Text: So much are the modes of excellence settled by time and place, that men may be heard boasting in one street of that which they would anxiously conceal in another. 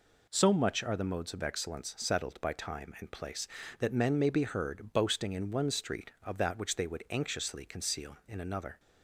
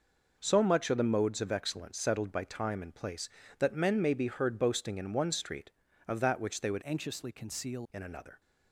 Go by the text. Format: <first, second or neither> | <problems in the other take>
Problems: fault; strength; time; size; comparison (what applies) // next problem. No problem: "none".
first | changes voice from "anxiously" to "conceal"; from 6.8 to 7.8 s; 1.0 s long